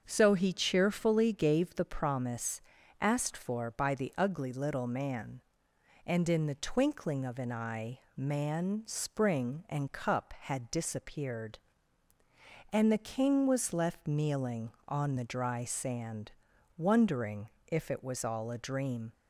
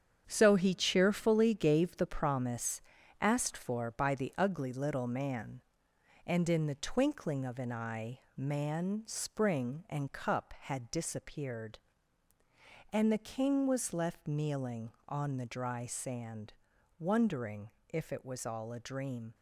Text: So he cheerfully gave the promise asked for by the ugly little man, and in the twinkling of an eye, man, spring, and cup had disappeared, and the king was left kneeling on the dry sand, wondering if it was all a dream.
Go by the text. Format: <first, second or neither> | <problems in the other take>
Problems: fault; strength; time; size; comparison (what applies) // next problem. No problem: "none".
first | gets quieter; strong; throughout; 8 dB // starts louder than the rest; strong; until 1.2 s; 8 dB; also in the first // pauses between "promise" and "asked"; at 2.8 s; 0.40 s long; also in the first // pauses between "wondering" and "if"; slight; at 17.7 s; 0.20 s long; slight in the first